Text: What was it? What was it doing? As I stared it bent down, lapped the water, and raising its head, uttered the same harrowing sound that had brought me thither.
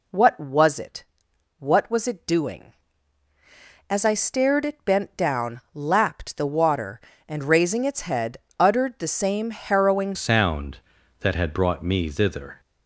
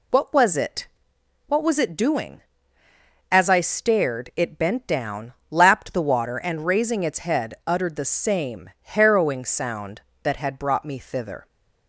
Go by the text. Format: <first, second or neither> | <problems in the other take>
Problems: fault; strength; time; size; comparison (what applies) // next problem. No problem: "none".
second | changes voice at "sound"; from 10.1 s on; 2.4 s long